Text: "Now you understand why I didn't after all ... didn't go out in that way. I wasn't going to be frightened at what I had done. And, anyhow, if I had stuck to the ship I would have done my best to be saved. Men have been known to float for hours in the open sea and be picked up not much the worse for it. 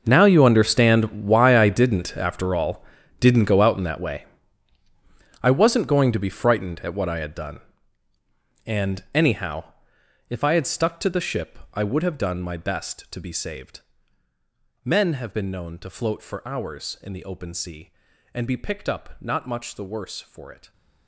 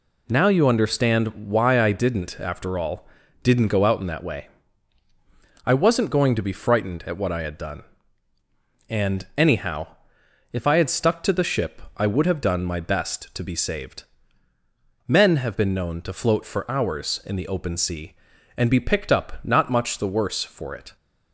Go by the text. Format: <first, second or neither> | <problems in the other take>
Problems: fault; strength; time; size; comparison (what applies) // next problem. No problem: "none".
second | gets quieter; strong; throughout; 18 dB // pauses between "ship" and "I"; slight; at 11.5 s; 0.16 s long; slight in the second